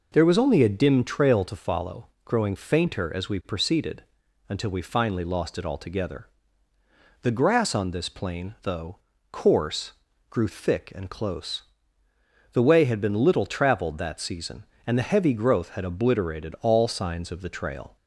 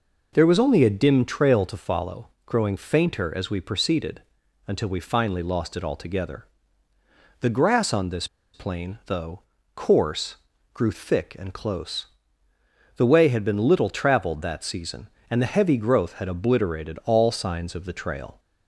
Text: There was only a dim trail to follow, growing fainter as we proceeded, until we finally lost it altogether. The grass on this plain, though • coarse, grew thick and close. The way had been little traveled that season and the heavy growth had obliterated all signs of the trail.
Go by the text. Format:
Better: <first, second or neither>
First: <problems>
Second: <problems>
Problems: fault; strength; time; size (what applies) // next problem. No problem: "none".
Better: first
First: none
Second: pauses between "this" and "plain"; slight; at 8.2 s; 0.27 s long